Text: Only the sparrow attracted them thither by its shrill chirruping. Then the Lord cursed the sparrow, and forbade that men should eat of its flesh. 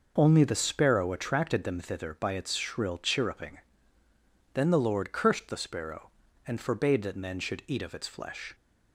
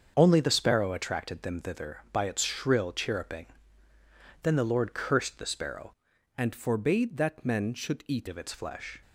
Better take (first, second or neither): first